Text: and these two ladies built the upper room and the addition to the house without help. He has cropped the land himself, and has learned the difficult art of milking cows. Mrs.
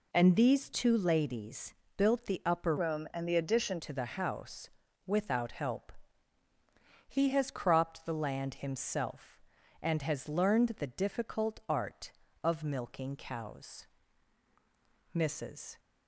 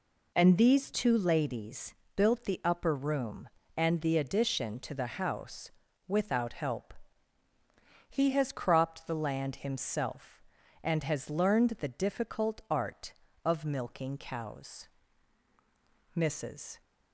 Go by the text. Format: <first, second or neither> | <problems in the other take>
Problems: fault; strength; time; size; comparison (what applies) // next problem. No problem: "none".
second | pauses between "ladies" and "built"; slight; at 1.7 s; 0.24 s long; slight in the second // changes voice from "room" to "addition"; from 2.7 to 3.7 s; 1.0 s long // pauses between "house" and "without"; slight; at 4.6 s; 0.36 s long; slight in the second